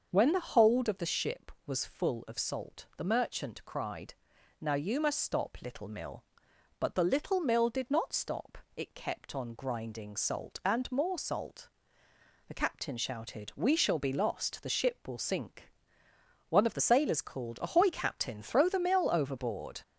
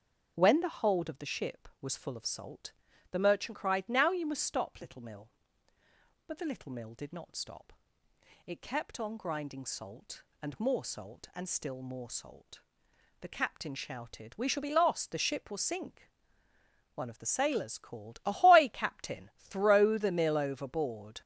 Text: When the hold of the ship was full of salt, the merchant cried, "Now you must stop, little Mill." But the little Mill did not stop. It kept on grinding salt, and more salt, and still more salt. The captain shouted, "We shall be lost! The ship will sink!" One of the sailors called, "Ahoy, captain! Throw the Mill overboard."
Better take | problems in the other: second | starts louder than the rest; until 1.1 s; 6.5 dB; also in the second // skips "and still more salt"; at 12.0 s

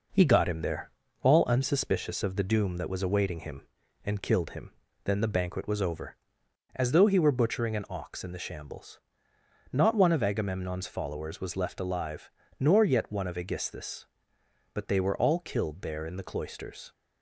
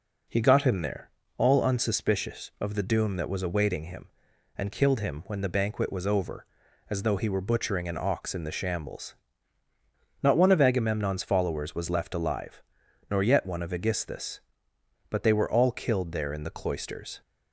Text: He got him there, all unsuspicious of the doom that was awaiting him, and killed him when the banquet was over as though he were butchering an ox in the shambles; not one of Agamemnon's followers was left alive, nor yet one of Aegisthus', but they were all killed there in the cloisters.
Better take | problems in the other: second | says "then" for "when"; at 5.0 s

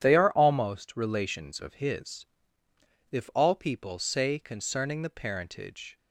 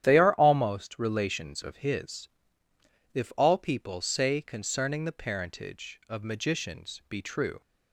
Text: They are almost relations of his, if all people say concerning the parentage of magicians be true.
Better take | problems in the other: second | starts louder than the rest; strong; until 1.0 s; 10 dB; strong in the second // stops before "of magicians be true"; at 5.9 s

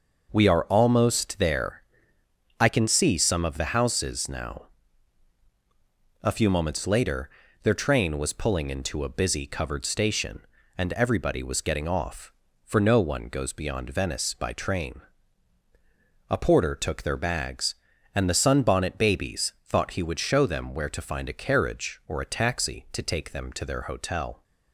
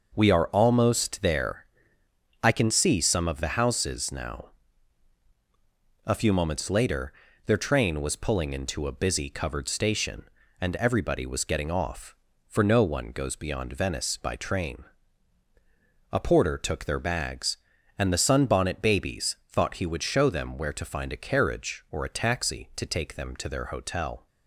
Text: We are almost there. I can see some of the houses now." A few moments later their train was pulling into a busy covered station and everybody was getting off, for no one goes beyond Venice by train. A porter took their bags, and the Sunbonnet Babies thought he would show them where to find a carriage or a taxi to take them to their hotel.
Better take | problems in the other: neither | pauses between "later" and "their"; slight; the same in both

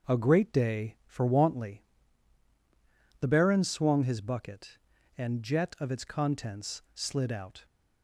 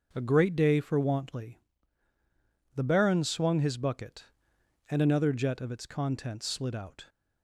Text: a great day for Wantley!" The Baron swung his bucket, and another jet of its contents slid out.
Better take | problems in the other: second | skips "another"; at 5.4 s

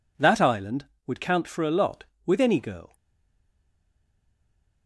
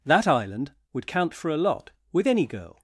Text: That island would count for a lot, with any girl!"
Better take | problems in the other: second | stays silent after the last word; noticeable; from 2.9 s on; 1.9 s long

